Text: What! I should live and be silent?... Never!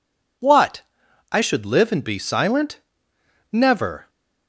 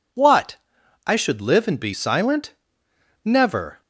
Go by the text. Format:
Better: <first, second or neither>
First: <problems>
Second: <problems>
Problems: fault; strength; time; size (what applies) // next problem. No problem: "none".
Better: neither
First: none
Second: none